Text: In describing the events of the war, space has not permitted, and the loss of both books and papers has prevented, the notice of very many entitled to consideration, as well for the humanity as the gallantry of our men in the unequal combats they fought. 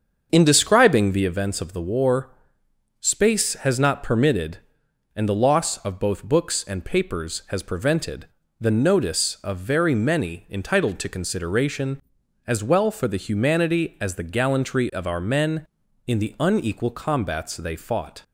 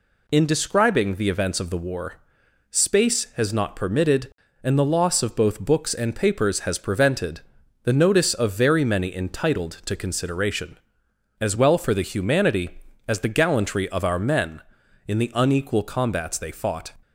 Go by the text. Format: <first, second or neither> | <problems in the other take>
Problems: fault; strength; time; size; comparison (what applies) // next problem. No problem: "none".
second | starts louder than the rest; until 1.4 s; 7 dB